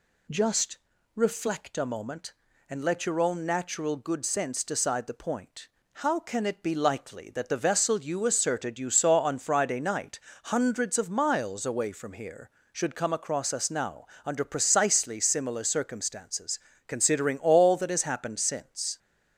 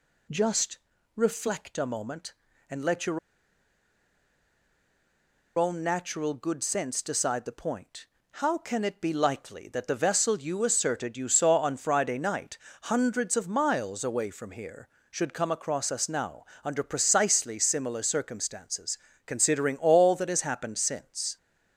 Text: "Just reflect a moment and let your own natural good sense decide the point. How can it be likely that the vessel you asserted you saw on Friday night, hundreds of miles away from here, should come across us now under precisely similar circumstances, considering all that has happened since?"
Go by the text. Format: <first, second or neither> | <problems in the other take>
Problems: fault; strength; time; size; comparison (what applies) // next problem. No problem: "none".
first | pauses between "Just" and "reflect"; at 0.7 s; 0.38 s long; also in the first // pauses between "your" and "own"; strong; at 3.1 s; 2.3 s long // pauses between "now" and "under"; slight; at 16.4 s; 0.20 s long; slight in the first